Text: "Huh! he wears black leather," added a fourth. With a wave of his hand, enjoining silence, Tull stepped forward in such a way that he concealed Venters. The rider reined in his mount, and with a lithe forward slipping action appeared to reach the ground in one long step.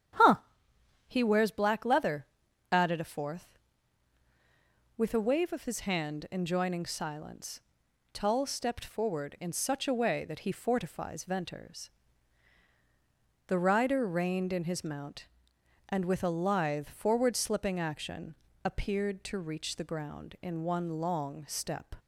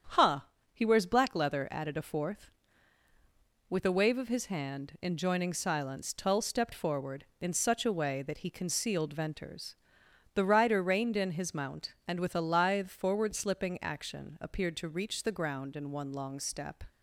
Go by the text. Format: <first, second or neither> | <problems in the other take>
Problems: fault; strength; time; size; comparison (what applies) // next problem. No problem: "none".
second | starts louder than the rest; strong; until 1.8 s; 9.5 dB; strong in the second // says "fortifies" for "concealed"; at 10.5 s // pauses between "action" and "appeared"; slight; at 18.3 s; 0.28 s long